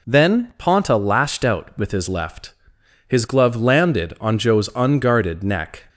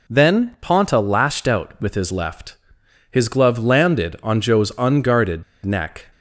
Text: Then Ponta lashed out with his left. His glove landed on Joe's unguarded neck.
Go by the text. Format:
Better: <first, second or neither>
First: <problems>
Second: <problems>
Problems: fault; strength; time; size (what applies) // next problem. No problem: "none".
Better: first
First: none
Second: pauses between "unguarded" and "neck"; slight; at 5.4 s; 0.21 s long